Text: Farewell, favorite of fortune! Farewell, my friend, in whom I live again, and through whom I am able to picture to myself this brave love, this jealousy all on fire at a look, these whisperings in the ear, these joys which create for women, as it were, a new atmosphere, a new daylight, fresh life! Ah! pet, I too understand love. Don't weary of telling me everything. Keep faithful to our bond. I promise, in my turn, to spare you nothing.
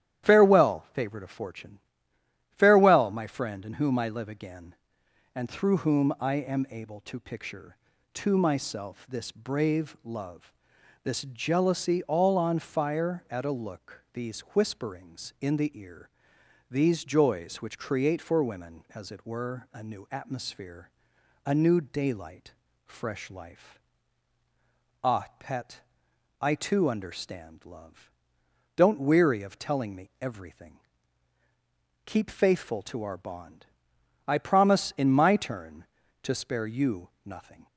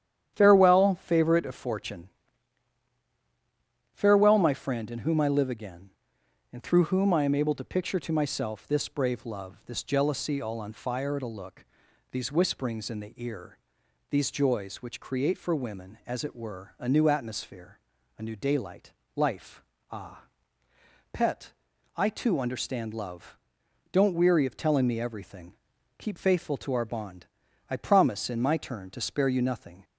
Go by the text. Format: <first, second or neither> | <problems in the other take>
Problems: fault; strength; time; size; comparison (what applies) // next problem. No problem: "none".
first | starts louder than the rest; strong; until 1.3 s; 10 dB; strong in the first // skips "fresh"; at 19.0 s